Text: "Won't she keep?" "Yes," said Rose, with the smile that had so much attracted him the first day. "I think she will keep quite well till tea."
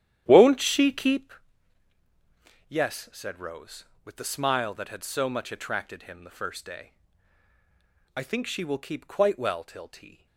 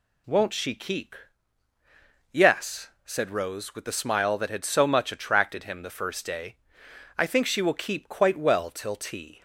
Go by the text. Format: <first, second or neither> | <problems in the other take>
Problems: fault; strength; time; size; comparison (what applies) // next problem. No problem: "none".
second | starts louder than the rest; strong; until 1.3 s; 11 dB